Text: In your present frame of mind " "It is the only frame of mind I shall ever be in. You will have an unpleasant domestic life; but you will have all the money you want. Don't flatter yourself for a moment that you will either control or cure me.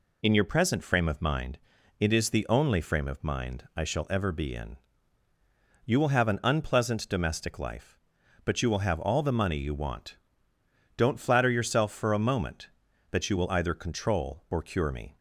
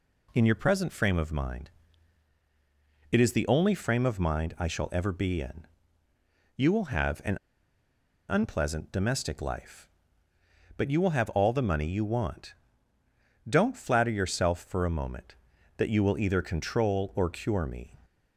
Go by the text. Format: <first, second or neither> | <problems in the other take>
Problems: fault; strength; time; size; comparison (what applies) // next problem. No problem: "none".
first | pauses between "an" and "unpleasant"; noticeable; at 7.3 s; 0.94 s long